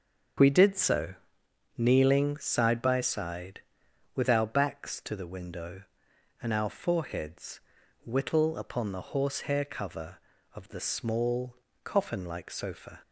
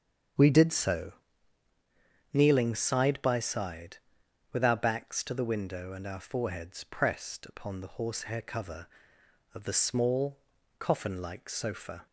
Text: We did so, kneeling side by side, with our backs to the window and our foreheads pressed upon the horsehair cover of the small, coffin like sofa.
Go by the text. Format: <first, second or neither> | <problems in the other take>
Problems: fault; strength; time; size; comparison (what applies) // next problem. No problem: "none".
second | starts louder than the rest; until 2.0 s; 7 dB; strong in the second // says "whittle" for "pressed"; at 8.0 s